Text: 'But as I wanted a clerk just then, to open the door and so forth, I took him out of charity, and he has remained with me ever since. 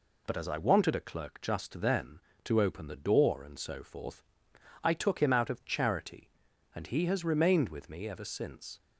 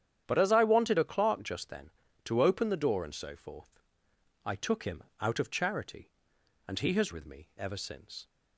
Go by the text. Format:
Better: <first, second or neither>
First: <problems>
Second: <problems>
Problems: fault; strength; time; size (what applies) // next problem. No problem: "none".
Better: first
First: none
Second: starts louder than the rest; strong; until 1.2 s; 9.5 dB // pauses between "him" and "out"; slight; at 5.0 s; 0.18 s long // skips "remained"; at 7.1 s